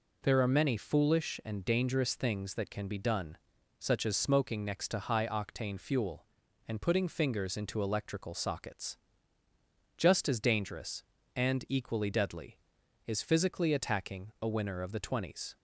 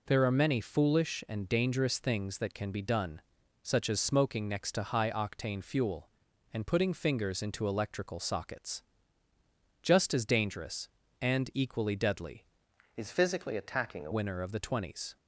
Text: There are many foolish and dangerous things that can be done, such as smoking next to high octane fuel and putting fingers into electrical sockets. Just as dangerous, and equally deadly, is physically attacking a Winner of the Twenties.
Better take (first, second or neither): first